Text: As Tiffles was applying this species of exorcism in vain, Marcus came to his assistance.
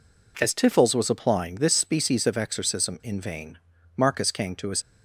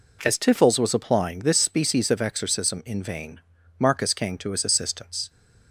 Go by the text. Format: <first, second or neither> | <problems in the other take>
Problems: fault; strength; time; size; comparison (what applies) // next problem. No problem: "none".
second | stops before "assistance"; at 4.8 s